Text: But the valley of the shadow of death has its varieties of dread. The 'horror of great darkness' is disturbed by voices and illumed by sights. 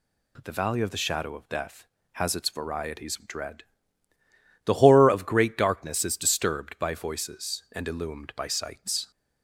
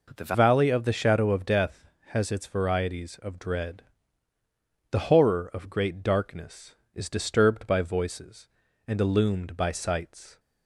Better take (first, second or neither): first